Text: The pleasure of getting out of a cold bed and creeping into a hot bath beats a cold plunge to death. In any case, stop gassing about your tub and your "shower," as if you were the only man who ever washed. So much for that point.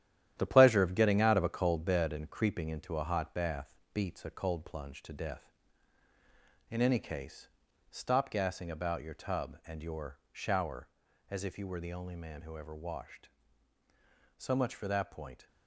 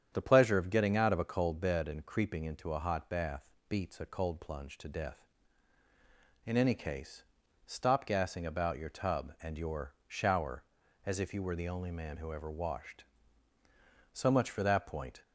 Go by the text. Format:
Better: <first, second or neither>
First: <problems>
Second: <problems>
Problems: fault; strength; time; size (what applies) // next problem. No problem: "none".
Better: second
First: gets quieter; strong; throughout; 7.5 dB // starts louder than the rest; strong; until 1.3 s; 11 dB // pauses between "bath" and "beats"; slight; at 3.7 s; 0.22 s long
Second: starts louder than the rest; strong; until 1.1 s; 8.5 dB // pauses between "bath" and "beats"; slight; at 3.4 s; 0.22 s long